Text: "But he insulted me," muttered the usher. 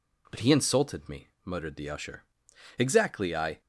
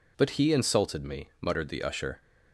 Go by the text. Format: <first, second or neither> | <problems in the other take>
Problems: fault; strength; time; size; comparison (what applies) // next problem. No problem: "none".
second | goes on to say "Exactly I"; noticeable; from 2.8 s on; 0.80 s long